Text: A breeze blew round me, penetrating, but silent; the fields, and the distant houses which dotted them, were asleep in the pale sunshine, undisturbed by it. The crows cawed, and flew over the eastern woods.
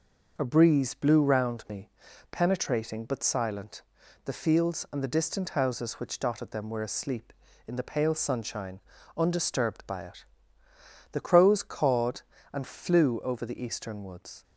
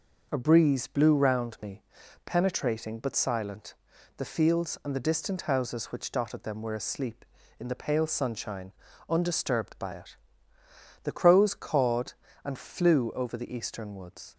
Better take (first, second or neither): neither